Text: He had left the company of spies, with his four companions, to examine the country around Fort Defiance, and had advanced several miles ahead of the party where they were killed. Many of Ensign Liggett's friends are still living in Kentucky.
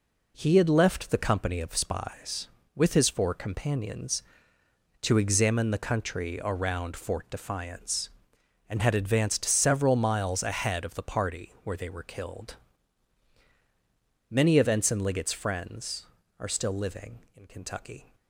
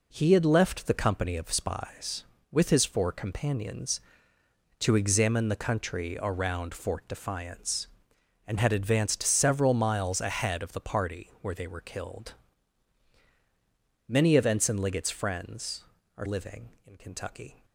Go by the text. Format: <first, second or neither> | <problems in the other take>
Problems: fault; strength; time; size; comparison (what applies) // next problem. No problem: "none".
first | skips "still"; at 16.2 s